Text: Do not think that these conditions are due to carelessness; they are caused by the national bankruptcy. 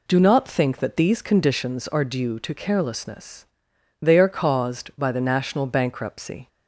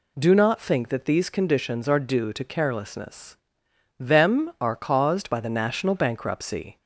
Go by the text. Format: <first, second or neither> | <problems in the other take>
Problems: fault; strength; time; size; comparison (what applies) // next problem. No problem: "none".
first | says "them" for "they"; at 3.9 s